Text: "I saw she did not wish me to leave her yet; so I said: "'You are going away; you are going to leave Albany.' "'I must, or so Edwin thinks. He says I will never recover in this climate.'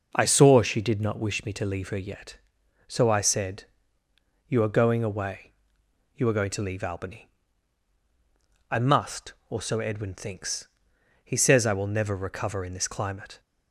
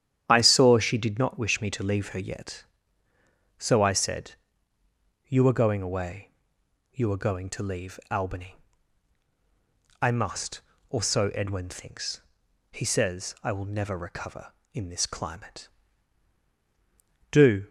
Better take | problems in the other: first | starts louder than the rest; strong; until 1.2 s; 10 dB // goes on to say "Do"; slight; from 17.3 s on; 0.38 s long

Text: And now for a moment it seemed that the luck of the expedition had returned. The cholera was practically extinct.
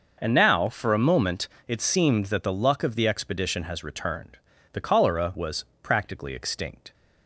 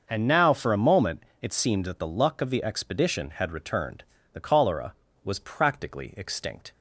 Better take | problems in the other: second | starts louder than the rest; noticeable; until 1.2 s; 6 dB; also in the second // pauses between "moment" and "it"; slight; at 1.4 s; 0.20 s long; slight in the second // says "has" for "had"; at 3.6 s // pauses between "was" and "practically"; slight; at 5.6 s; 0.16 s long

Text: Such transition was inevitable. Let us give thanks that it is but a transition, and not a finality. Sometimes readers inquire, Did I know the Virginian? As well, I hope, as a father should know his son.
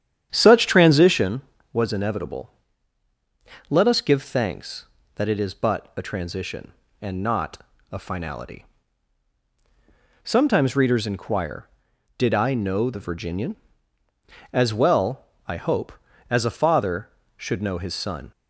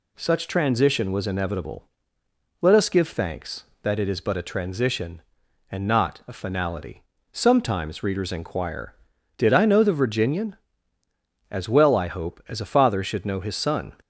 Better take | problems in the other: second | starts louder than the rest; strong; until 1.3 s; 9.5 dB // pauses between "not" and "a"; slight; at 7.6 s; 0.30 s long

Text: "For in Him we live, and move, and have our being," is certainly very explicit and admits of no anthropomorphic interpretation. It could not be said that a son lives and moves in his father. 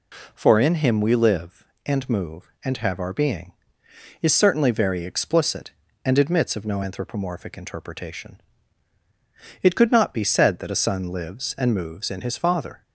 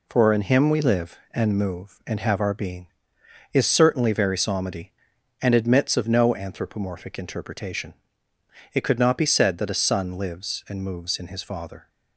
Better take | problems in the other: first | says "psalmody" for "explicit"; at 4.3 s

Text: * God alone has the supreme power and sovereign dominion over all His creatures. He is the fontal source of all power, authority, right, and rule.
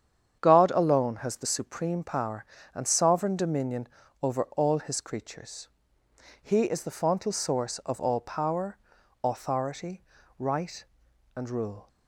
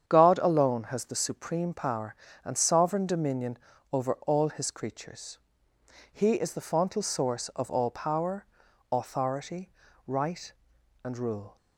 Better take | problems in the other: neither | starts louder than the rest; strong; the same in both // pauses between "dominion" and "over"; slight; the same in both

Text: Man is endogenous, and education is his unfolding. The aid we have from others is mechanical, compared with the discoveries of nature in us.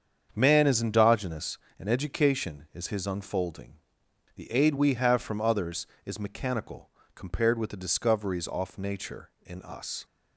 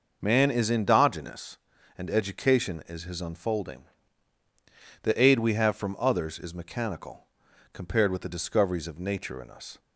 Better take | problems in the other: second | starts louder than the rest; strong; until 1.3 s; 7.5 dB // says "off" for "of"; at 8.4 s

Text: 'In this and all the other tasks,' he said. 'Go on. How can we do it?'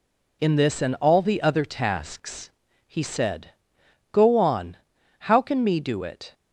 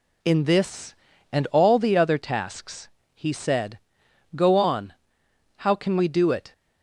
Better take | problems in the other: second | says "me" for "we"; at 5.6 s

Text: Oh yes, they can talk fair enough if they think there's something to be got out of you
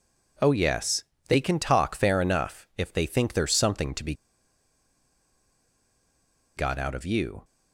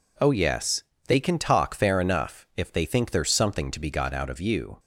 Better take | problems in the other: second | pauses between "be" and "got"; strong; at 4.1 s; 2.4 s long

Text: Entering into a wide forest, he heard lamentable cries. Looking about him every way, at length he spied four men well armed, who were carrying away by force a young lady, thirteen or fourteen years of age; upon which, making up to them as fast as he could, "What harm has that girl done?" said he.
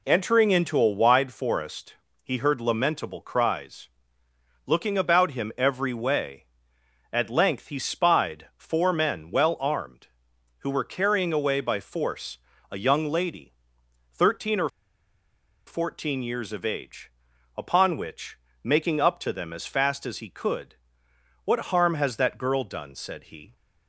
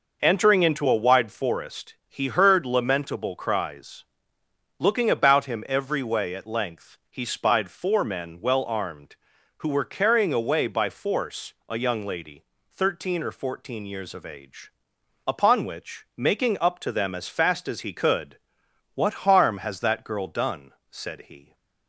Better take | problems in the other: second | pauses between "force" and "a"; slight; at 12.3 s; 0.34 s long; slight in the second // pauses between "or" and "fourteen"; noticeable; at 14.6 s; 0.97 s long

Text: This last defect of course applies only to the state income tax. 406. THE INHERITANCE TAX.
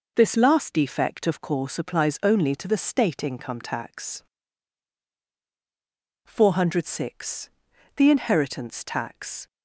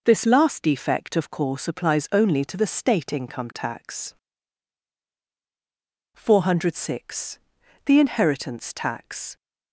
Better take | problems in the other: neither | none

